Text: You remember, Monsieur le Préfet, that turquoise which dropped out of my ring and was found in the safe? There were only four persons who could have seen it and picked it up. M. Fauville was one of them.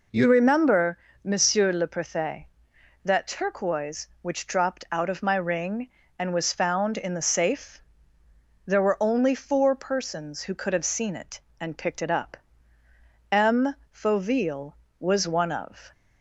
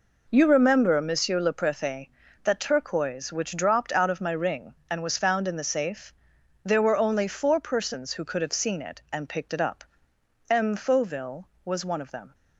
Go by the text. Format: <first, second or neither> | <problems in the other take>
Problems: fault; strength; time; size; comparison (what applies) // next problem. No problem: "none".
second | stops before "them"; at 15.9 s